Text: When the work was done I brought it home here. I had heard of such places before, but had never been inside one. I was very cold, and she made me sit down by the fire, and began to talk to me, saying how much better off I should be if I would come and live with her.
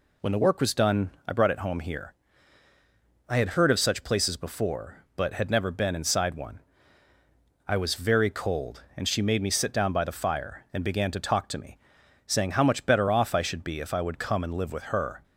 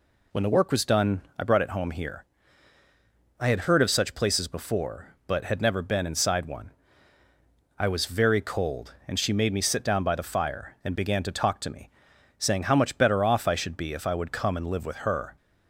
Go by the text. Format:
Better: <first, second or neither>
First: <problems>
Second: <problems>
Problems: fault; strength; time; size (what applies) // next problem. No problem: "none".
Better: neither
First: pauses between "done" and "I"; slight; at 1.1 s; 0.16 s long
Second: pauses between "done" and "I"; slight; at 1.2 s; 0.16 s long